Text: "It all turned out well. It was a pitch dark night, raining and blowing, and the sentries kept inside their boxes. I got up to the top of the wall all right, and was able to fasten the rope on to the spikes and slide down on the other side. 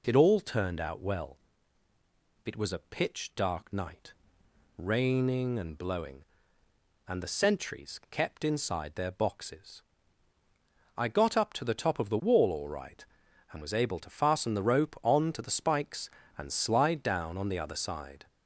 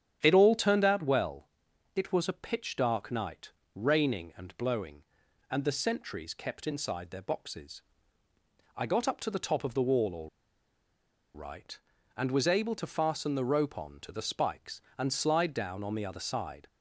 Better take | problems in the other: first | starts louder than the rest; strong; until 1.2 s; 9.5 dB // pauses between "all" and "right"; at 10.2 s; 1.0 s long

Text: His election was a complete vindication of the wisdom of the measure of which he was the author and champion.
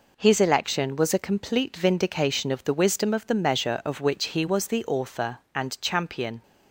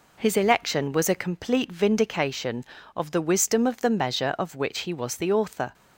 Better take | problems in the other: first | stops before "and champion"; at 5.7 s

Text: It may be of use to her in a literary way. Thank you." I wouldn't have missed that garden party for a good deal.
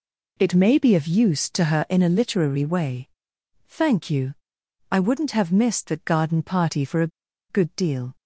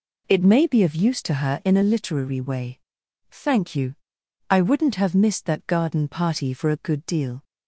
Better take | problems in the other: second | pauses between "a" and "good"; at 7.1 s; 0.40 s long

